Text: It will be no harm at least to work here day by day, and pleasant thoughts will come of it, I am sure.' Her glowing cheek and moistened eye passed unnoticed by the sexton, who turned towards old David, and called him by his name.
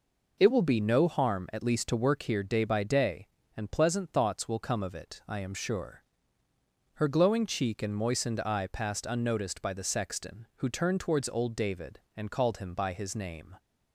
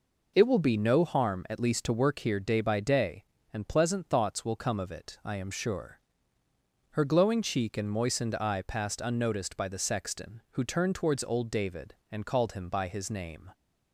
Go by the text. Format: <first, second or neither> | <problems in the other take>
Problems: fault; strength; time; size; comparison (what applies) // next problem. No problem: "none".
neither | none